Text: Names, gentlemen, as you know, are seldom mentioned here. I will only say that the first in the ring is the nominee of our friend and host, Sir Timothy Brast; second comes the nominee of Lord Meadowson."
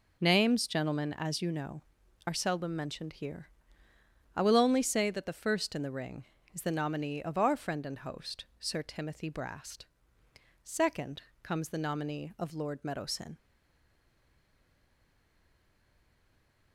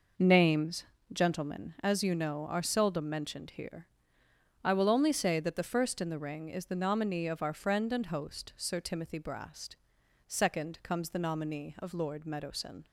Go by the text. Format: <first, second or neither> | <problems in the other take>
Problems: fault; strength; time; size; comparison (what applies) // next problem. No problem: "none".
second | pauses between "second" and "comes"; slight; at 11.2 s; 0.22 s long // stays silent after the last word; strong; from 13.3 s on; 3.4 s long